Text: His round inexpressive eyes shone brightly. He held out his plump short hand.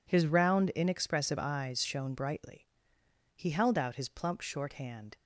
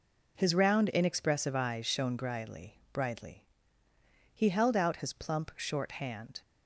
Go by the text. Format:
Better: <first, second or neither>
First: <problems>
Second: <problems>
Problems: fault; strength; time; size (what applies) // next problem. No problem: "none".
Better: first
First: none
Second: says "brightly" twice; at 2.9 s